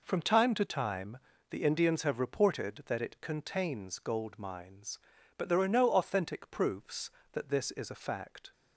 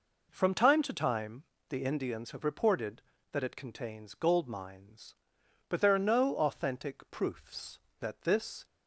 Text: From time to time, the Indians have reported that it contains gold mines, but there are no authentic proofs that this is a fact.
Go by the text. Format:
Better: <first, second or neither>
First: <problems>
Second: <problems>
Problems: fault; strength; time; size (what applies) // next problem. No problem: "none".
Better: first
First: none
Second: stops before "is a fact"; at 8.6 s